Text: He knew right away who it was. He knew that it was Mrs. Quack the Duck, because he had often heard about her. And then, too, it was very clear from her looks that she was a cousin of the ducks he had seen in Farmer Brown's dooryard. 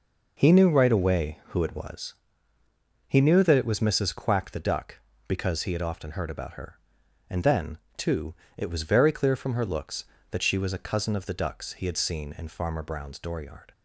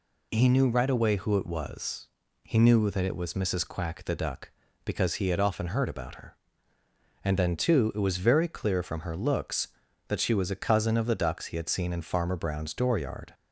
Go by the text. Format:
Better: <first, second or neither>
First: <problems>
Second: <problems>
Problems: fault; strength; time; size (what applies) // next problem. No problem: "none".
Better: neither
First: none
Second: none